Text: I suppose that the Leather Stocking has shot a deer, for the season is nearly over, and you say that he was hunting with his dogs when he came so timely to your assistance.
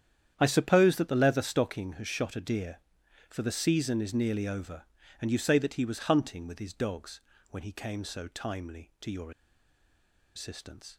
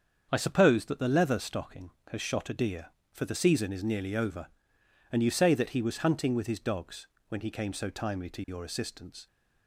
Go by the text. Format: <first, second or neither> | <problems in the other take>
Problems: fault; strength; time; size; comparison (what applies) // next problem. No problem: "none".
second | starts louder than the rest; strong; until 1.3 s; 9.5 dB; also in the second // pauses between "dogs" and "when"; slight; at 7.2 s; 0.30 s long; slight in the second // pauses between "your" and "assistance"; at 9.3 s; 1.0 s long